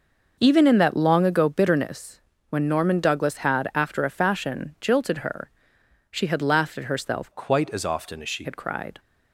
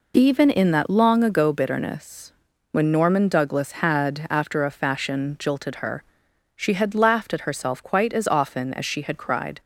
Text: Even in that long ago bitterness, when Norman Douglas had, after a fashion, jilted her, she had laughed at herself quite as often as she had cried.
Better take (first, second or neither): second